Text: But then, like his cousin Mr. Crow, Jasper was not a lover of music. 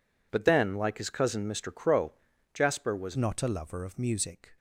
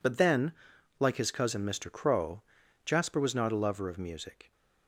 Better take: second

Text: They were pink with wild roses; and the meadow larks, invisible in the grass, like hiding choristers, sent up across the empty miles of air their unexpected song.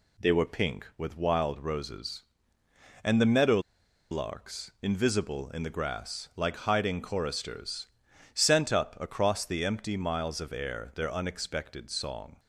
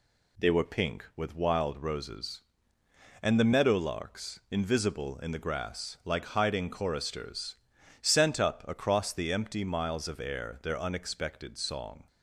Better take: second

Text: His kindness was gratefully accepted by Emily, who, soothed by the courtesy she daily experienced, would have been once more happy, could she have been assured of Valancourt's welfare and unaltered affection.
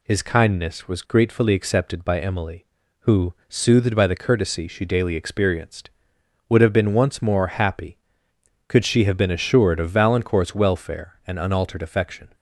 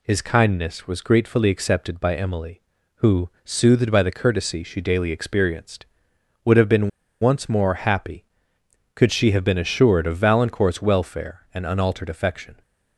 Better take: first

